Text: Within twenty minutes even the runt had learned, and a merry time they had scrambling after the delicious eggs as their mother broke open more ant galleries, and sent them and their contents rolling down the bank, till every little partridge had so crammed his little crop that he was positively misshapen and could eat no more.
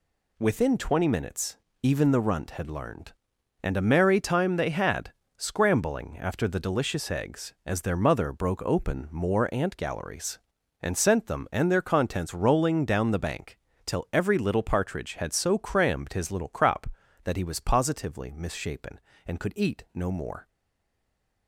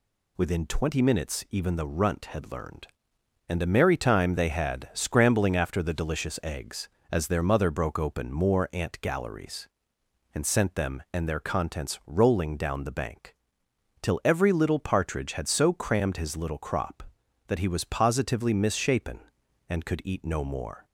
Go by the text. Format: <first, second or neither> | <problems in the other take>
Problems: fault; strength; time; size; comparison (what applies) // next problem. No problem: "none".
second | pauses between "minutes" and "even"; slight; at 1.5 s; 0.26 s long // pauses between "had" and "scrambling"; slight; at 5.1 s; 0.24 s long // stays silent after the last word; from 20.4 s on; 1.0 s long